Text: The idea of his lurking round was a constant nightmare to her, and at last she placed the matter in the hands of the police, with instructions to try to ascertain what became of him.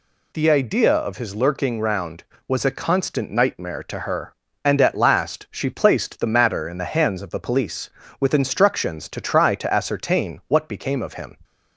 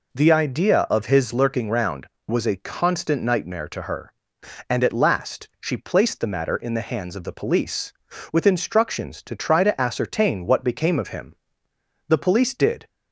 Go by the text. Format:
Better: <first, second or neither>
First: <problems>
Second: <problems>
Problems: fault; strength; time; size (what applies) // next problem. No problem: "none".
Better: first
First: none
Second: goes on to say "The police did"; noticeable; from 12.0 s on; 0.80 s long